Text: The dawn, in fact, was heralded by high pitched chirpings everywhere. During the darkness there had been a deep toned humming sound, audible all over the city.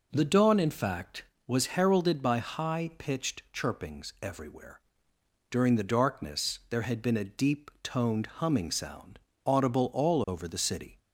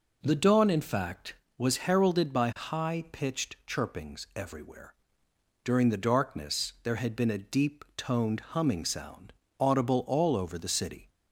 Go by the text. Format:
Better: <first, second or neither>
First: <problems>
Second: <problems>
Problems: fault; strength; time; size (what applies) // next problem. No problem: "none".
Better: neither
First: none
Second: none